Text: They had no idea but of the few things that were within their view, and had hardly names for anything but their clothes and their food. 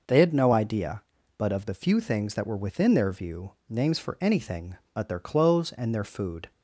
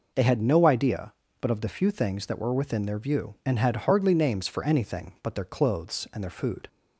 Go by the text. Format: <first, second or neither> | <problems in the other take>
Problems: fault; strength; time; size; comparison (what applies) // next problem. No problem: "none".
second | skips "and had hardly"; at 3.6 s